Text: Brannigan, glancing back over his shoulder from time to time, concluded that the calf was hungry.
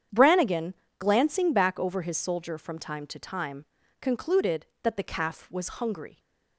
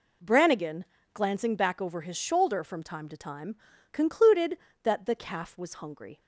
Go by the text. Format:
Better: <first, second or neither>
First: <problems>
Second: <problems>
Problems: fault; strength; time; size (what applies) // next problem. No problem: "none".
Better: second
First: starts louder than the rest; strong; until 1.3 s; 8.5 dB // says "soldier" for "shoulder"; at 2.1 s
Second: none